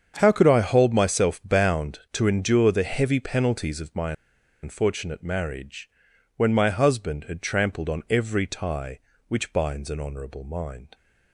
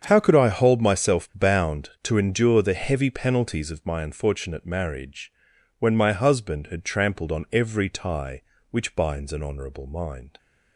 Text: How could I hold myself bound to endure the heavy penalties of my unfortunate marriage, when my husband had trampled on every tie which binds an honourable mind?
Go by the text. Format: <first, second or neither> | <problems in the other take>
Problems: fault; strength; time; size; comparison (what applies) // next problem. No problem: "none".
second | starts louder than the rest; strong; until 1.1 s; 7.5 dB; strong in the second // pauses between "my" and "unfortunate"; noticeable; at 4.1 s; 0.50 s long